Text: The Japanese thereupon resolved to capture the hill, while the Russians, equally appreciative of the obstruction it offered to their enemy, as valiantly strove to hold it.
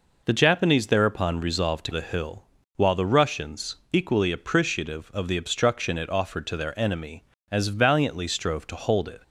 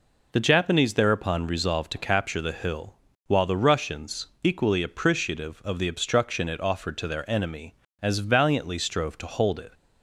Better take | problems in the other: second | skips "capture"; at 1.9 s

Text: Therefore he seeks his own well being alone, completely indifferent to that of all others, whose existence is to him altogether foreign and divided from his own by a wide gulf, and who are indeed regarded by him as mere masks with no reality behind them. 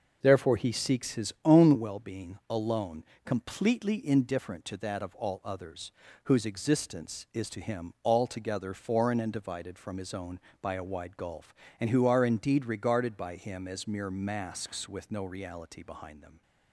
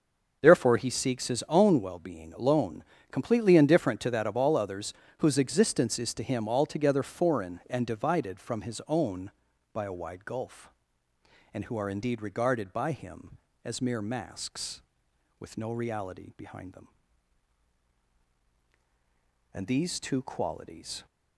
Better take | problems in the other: first | starts louder than the rest; noticeable; until 1.4 s; 6 dB // goes on to say "And these two qualities"; from 19.5 s on; 1.5 s long

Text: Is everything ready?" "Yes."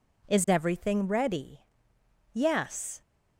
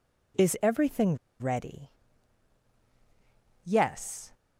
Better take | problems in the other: first | pauses between "everything" and "ready"; slight; at 1.1 s; 0.24 s long

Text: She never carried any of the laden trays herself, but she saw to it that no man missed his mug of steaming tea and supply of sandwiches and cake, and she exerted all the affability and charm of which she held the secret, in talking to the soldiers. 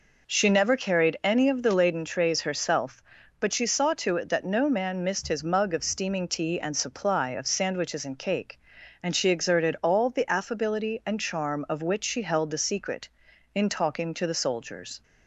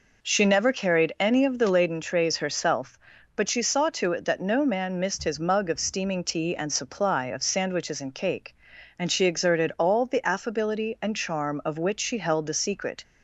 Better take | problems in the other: first | stops before "in talking to the soldiers"; at 13.0 s

